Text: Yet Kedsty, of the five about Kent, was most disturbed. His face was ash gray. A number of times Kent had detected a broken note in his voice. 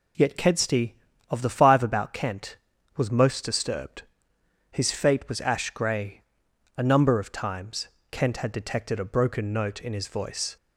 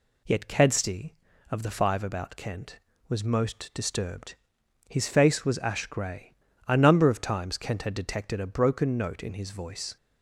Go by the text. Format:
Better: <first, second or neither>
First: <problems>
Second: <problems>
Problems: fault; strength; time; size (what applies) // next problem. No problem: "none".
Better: second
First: says "fate" for "face"; at 4.8 s // pauses between "times" and "Kent"; slight; at 7.8 s; 0.22 s long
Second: none